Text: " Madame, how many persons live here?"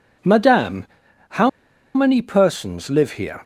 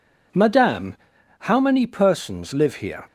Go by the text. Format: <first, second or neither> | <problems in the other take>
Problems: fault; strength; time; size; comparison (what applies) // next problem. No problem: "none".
second | pauses between "how" and "many"; noticeable; at 1.4 s; 0.46 s long